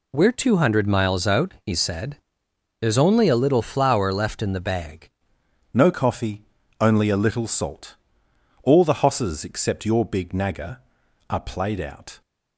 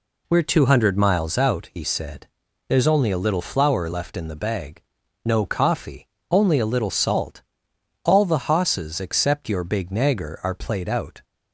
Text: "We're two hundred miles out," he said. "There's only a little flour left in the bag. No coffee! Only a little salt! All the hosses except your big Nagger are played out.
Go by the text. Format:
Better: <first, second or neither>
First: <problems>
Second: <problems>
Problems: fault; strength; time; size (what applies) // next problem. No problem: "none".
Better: second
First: changes voice at "No"; from 5.7 s on; 6.5 s long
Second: none